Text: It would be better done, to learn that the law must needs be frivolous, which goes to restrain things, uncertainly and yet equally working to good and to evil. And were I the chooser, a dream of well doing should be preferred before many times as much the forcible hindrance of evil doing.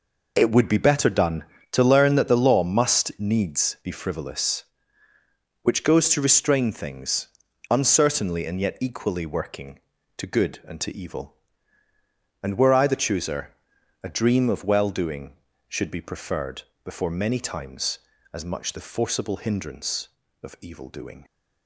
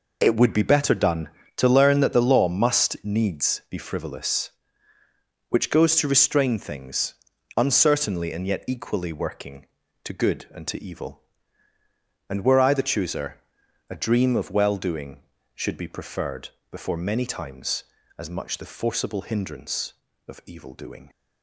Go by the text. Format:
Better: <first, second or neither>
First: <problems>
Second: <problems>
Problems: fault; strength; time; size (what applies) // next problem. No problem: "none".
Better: neither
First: pauses between "preferred" and "before"; slight; at 16.6 s; 0.20 s long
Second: pauses between "preferred" and "before"; slight; at 16.5 s; 0.20 s long